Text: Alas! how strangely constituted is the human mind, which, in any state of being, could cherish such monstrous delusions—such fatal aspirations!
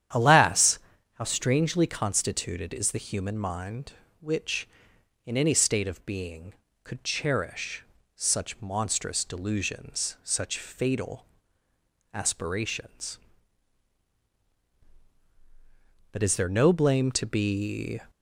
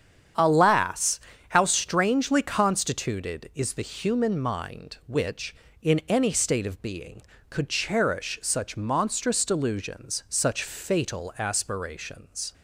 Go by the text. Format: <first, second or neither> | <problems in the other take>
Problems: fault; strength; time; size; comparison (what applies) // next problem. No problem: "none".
second | starts louder than the rest; strong; until 1.5 s; 10 dB; strong in the second // pauses between "cherish" and "such"; slight; at 7.8 s; 0.32 s long // pauses between "fatal" and "aspirations"; noticeable; at 11.2 s; 0.88 s long // goes on to say "But is there no blame to be"; strong; from 16.0 s on; 1.9 s long